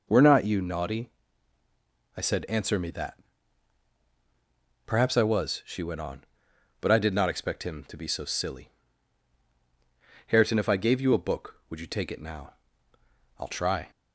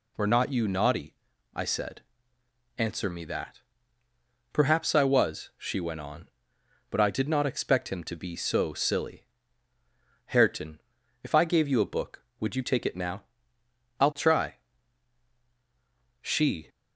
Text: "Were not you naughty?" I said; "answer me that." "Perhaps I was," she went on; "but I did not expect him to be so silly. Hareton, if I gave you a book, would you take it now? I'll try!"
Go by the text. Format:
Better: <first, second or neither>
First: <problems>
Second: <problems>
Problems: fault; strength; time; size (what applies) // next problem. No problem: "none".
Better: first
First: none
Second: goes on to say "She"; slight; from 16.2 s on; 0.48 s long